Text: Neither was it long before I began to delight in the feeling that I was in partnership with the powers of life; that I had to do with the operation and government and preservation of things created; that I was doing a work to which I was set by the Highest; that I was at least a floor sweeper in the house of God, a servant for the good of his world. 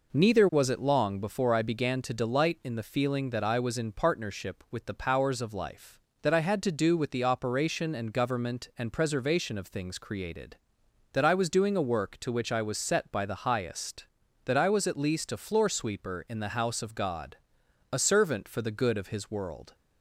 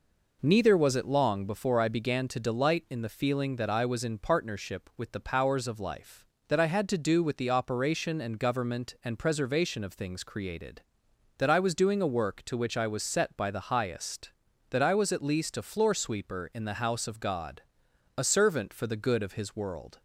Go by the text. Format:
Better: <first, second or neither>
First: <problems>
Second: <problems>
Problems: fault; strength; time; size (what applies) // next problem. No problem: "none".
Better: neither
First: none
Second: none